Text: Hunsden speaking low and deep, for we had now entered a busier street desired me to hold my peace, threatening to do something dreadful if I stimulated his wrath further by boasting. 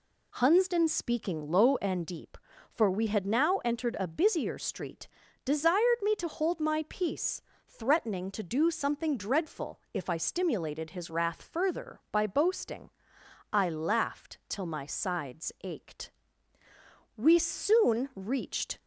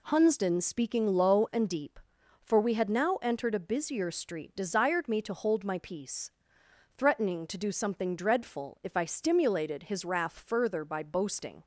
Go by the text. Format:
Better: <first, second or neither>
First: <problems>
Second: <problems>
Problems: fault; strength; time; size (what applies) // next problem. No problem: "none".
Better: second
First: pauses between "street" and "desired"; slight; at 5.0 s; 0.36 s long // goes on to say "I laughed till my sides ached We soon reached"; strong; from 13.5 s on; 5.2 s long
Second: none